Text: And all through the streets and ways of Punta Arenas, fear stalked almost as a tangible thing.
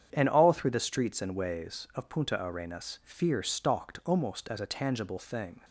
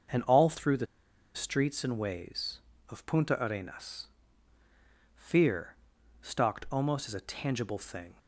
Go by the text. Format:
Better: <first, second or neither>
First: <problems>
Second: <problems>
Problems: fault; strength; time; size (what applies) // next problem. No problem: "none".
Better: first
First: starts louder than the rest; strong; until 1.1 s; 8 dB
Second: starts louder than the rest; until 1.6 s; 6.5 dB // pauses between "the" and "streets"; noticeable; at 0.8 s; 0.49 s long // pauses between "fear" and "stalked"; at 5.7 s; 0.44 s long